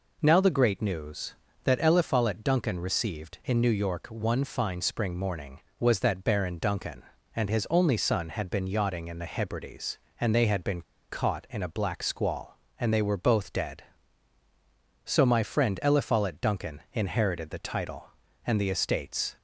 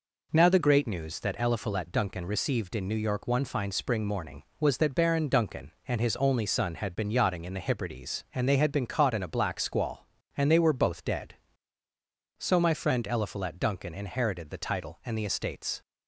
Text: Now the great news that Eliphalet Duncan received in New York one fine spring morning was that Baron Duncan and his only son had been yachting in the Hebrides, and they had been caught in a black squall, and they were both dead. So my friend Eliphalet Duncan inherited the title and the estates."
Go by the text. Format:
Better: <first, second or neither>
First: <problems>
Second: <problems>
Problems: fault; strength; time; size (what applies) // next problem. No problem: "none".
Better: second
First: pauses between "been" and "caught"; slight; at 10.8 s; 0.28 s long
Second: none